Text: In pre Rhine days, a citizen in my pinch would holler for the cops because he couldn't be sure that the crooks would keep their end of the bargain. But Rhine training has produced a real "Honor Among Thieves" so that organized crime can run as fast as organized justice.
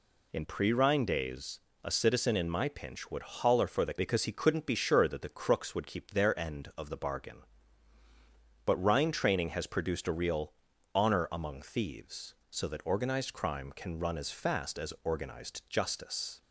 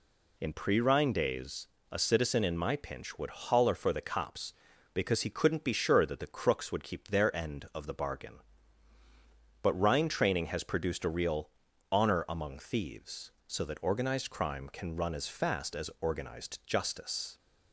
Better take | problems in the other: second | skips "cops"; at 3.9 s // pauses between "real" and "Honor"; at 10.5 s; 0.40 s long; also in the second

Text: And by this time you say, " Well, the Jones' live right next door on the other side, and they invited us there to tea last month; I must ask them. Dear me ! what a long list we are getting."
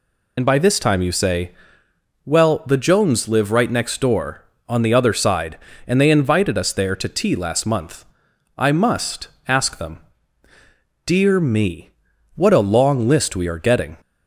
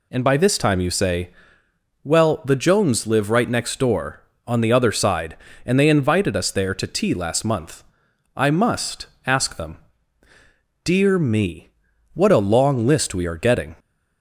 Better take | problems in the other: second | loses the start of "And"; at 0.3 s; 55 ms // pauses between "must" and "ask"; slight; at 9.2 s; 0.18 s long; slight in the second

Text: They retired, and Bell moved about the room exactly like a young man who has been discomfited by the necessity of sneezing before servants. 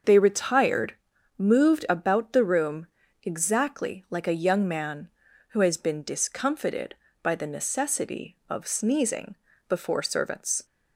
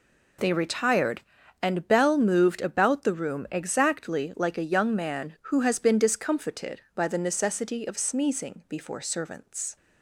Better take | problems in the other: second | starts louder than the rest; until 1.4 s; 6.5 dB // skips "and Bell"; at 1.1 s // pauses between "room" and "exactly"; at 2.8 s; 0.38 s long // pauses between "sneezing" and "before"; slight; at 9.3 s; 0.32 s long

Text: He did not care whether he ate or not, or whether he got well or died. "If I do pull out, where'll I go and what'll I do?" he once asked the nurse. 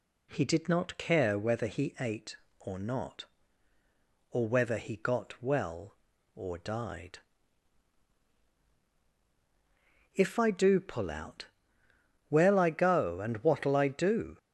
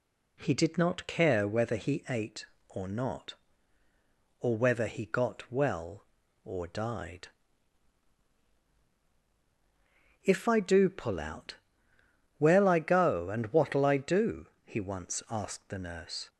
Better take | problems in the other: second | stops before "he once asked the nurse"; at 14.3 s

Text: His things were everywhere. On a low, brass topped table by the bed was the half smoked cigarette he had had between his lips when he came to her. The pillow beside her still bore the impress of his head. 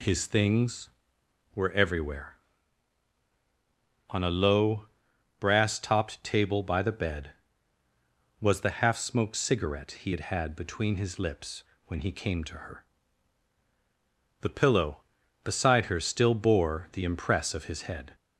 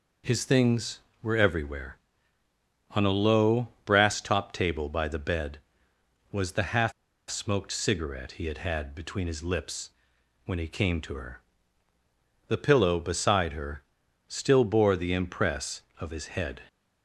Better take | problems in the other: first | pauses between "half" and "smoked"; at 6.9 s; 0.38 s long // pauses between "lips" and "when"; noticeable; at 9.8 s; 0.56 s long; slight in the first // pauses between "her" and "still"; noticeable; at 13.8 s; 0.46 s long

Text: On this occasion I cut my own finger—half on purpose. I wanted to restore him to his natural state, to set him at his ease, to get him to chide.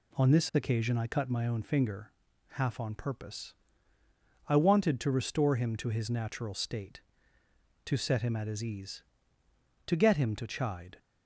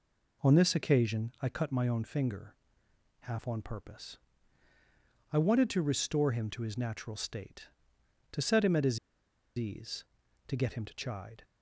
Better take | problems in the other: first | pauses between "his" and "ease"; noticeable; at 8.9 s; 0.60 s long

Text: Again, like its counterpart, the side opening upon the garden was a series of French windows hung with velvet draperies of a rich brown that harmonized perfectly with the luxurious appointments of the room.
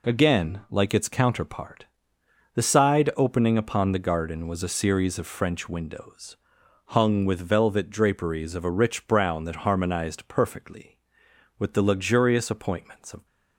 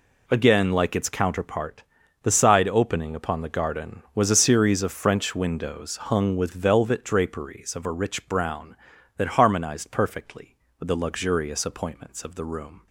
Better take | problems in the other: second | pauses between "windows" and "hung"; noticeable; at 6.3 s; 0.52 s long // stops before "the room"; at 13.2 s

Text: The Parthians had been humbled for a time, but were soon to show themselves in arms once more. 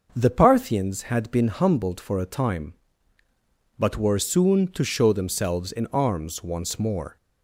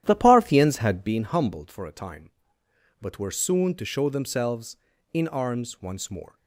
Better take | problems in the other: first | starts louder than the rest; strong; until 1.2 s; 11.5 dB

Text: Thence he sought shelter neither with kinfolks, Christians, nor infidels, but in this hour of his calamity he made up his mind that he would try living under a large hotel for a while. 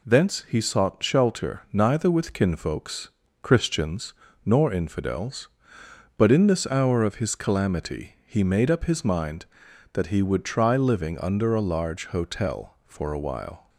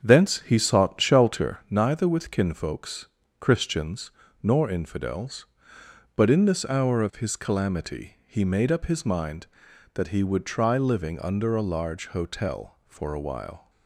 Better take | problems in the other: first | starts louder than the rest; strong; until 1.7 s; 8 dB

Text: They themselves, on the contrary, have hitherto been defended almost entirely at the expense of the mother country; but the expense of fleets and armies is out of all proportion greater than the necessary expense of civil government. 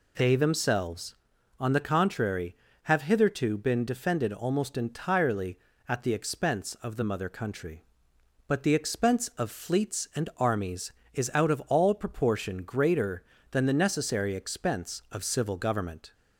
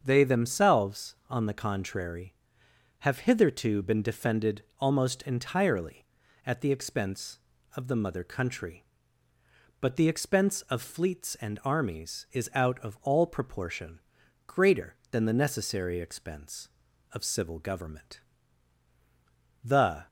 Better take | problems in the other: first | starts louder than the rest; until 1.0 s; 7 dB // pauses between "defended" and "almost"; slight; at 4.6 s; 0.16 s long // pauses between "proportion" and "greater"; noticeable; at 13.9 s; 0.48 s long // goes on to say "The"; slight; from 19.6 s on; 0.44 s long

